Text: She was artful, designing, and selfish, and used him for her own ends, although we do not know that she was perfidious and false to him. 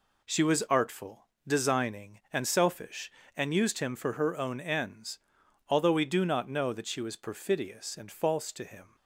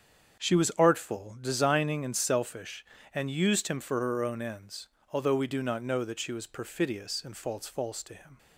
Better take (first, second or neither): first